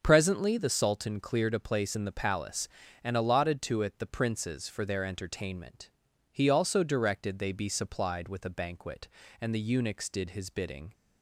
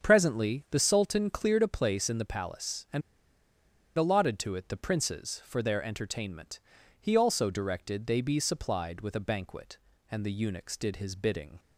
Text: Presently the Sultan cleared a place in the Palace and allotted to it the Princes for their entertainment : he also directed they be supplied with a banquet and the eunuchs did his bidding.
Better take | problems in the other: first | starts louder than the rest; until 1.1 s; 7 dB; also in the first // pauses between "and" and "allotted"; noticeable; at 3.0 s; 0.96 s long

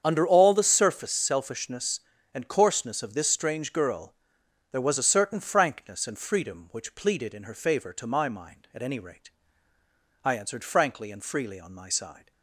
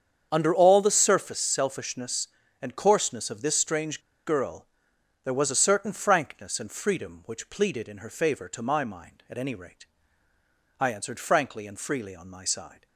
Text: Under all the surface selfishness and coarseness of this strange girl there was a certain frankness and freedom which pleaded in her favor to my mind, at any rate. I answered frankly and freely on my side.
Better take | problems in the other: first | starts louder than the rest; strong; until 1.3 s; 8 dB; strong in the first // pauses between "strange" and "girl"; slight; at 3.9 s; 0.26 s long // pauses between "girl" and "there"; noticeable; at 4.6 s; 0.56 s long; noticeable in the first

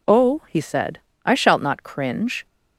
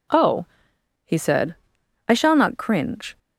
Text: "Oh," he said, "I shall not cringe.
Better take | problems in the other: second | says "shalt" for "shall"; at 1.3 s

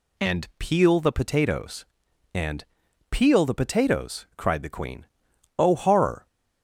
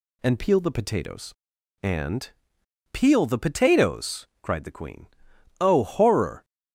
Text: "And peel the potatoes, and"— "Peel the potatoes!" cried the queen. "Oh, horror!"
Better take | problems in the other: neither | none

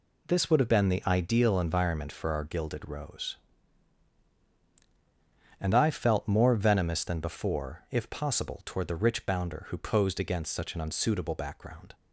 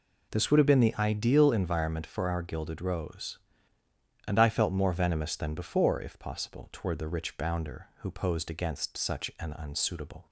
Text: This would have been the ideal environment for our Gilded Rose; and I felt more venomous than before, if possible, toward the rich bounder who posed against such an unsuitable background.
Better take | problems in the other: first | stops before "background"; at 10.2 s

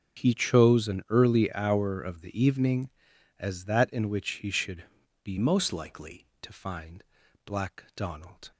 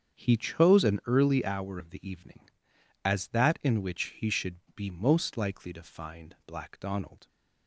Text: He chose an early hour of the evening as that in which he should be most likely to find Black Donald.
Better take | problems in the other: second | starts louder than the rest; until 1.2 s; 7 dB; strong in the second // pauses between "should" and "be"; at 4.8 s; 0.38 s long; slight in the second // changes voice from "most" to "likely"; from 5.3 to 6.2 s; 0.9 s long // pauses between "find" and "Black"; at 7.0 s; 0.40 s long

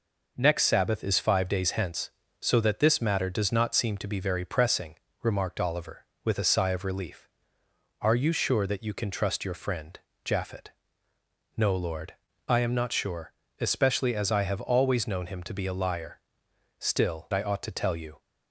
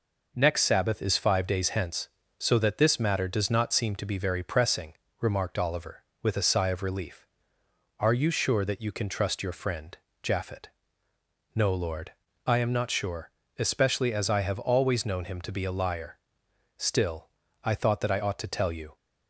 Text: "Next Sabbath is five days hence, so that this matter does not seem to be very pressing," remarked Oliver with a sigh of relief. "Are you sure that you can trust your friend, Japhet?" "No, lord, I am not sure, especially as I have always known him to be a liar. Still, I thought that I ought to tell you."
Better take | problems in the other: second | skips "I thought that"; at 17.3 s

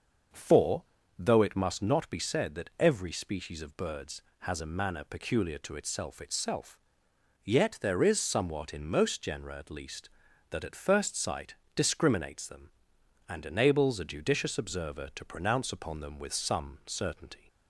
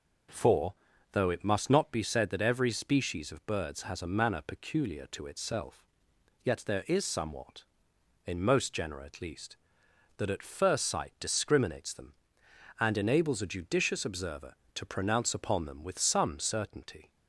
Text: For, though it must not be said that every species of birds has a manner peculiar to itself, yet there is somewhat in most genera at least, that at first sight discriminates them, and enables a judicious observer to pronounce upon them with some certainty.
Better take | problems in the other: second | starts louder than the rest; until 1.6 s; 6.5 dB // says "itself" twice; at 6.2 s // pauses between "sight" and "discriminates"; slight; at 11.5 s; 0.20 s long

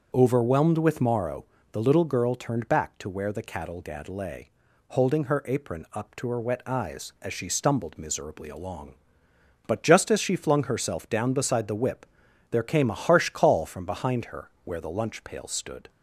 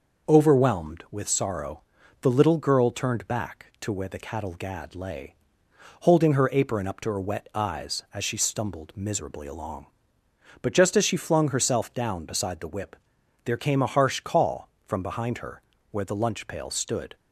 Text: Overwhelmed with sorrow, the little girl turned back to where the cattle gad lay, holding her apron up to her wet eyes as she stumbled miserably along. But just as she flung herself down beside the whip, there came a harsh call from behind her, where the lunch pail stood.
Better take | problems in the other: second | starts louder than the rest; until 1.1 s; 6.5 dB // says "morrow" for "sorrow"; at 1.0 s

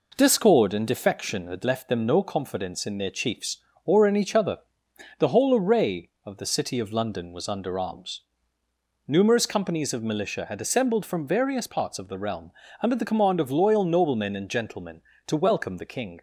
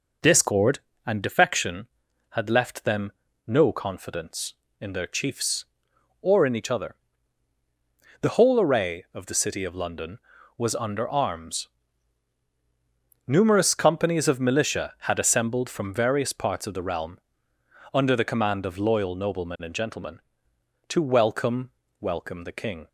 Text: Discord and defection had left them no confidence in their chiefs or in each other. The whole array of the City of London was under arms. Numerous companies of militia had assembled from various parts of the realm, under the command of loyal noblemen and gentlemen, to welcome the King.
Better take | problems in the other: first | pauses between "them" and "no"; slight; at 3.0 s; 0.36 s long // says "welcome" twice; at 21.9 s

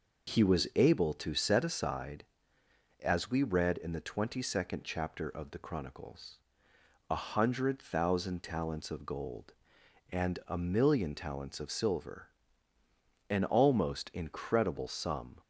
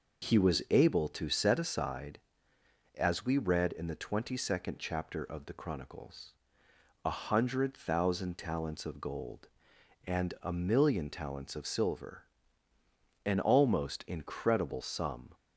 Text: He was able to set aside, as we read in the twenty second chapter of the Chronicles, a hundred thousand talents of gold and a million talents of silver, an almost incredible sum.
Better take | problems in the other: neither | none

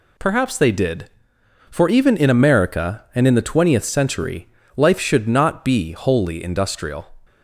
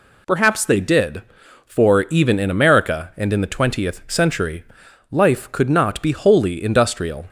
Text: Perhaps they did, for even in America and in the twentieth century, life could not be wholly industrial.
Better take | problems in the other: second | says "should" for "could"; at 4.9 s

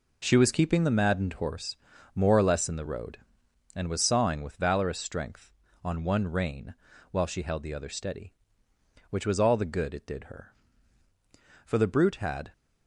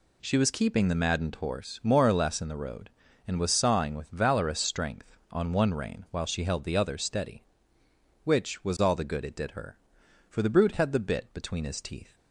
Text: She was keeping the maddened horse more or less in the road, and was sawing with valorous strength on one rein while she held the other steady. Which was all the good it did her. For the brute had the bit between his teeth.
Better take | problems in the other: second | pauses between "horse" and "more"; at 1.7 s; 0.40 s long // pauses between "rein" and "while"; slight; at 6.7 s; 0.36 s long // stops before "the bit between his teeth"; at 12.5 s

